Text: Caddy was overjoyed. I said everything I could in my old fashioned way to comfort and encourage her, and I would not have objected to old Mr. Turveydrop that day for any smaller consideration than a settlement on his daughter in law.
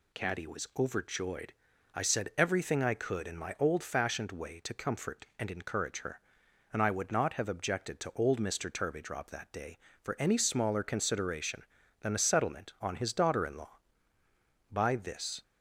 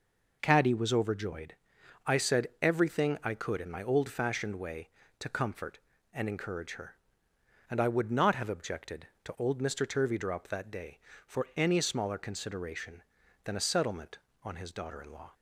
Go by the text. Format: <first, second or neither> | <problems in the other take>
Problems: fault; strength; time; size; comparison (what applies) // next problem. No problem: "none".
second | goes on to say "By this"; noticeable; from 14.7 s on; 0.70 s long